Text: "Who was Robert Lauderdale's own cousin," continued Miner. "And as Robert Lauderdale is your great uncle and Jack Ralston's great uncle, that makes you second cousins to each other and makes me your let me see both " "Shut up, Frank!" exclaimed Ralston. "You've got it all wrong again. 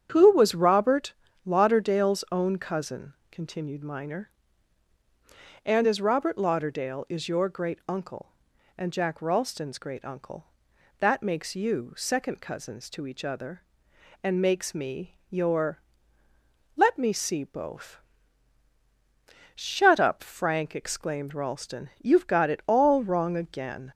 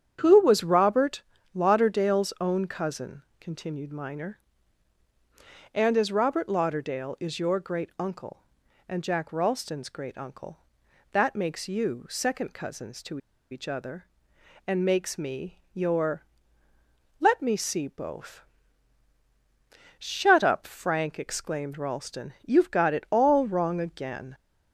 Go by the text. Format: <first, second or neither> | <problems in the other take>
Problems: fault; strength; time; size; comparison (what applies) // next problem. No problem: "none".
first | starts louder than the rest; strong; until 1.2 s; 8 dB; strong in the first // pauses between "Robert" and "Lauderdale's"; slight; at 1.2 s; 0.32 s long; slight in the first // pauses between "to" and "each"; slight; at 13.1 s; 0.33 s long // pauses between "your" and "let"; noticeable; at 16.2 s; 0.96 s long; noticeable in the first